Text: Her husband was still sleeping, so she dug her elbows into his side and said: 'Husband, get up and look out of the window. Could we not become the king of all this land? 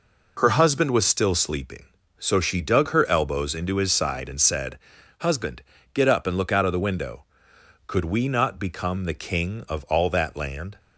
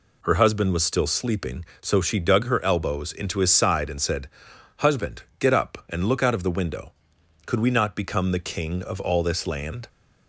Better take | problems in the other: second | says "that" for "this"; at 10.0 s

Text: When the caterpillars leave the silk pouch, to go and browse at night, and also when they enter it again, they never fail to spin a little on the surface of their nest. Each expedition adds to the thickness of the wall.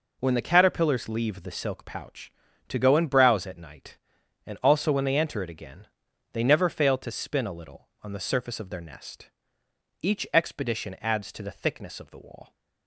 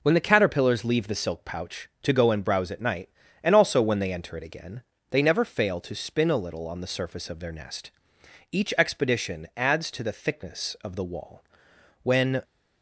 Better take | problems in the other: first | goes on to say "When"; slight; from 12.0 s on; 0.38 s long

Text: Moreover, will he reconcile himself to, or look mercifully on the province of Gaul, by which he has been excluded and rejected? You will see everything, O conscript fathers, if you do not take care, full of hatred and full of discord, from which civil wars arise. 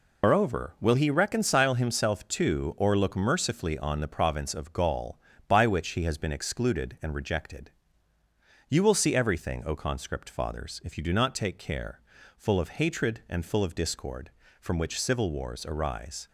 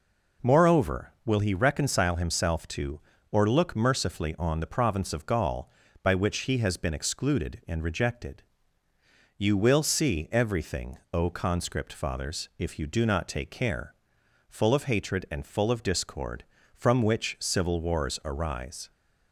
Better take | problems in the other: second | loses the start of "Moreover"; at 0.2 s; 145 ms

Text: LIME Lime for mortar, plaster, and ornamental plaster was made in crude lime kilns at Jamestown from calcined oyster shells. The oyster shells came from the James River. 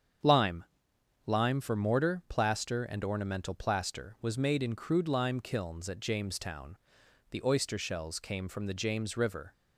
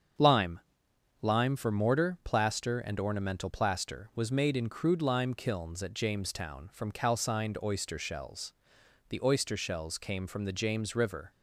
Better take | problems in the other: second | starts louder than the rest; strong; until 1.8 s; 7.5 dB; strong in the second // pauses between "LIME" and "Lime"; noticeable; at 0.6 s; 0.62 s long; noticeable in the second // skips "from calcined oyster shells"; at 7.0 s

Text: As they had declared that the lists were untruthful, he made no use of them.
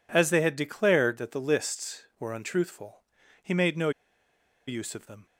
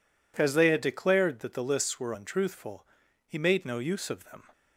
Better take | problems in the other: second | pauses between "no" and "use"; noticeable; at 3.8 s; 0.77 s long

